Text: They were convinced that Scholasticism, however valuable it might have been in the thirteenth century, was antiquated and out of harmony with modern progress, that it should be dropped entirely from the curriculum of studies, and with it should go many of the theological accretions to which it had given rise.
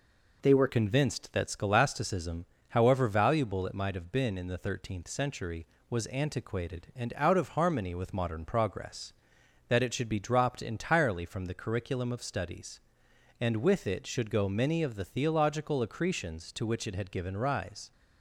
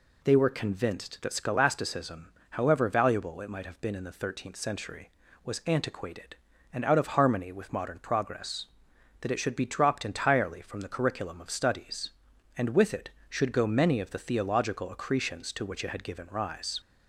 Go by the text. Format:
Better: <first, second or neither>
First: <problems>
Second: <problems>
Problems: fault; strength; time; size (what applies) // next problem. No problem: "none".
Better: second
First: changes voice at "convinced"; from 0.6 s on; 17.3 s long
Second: none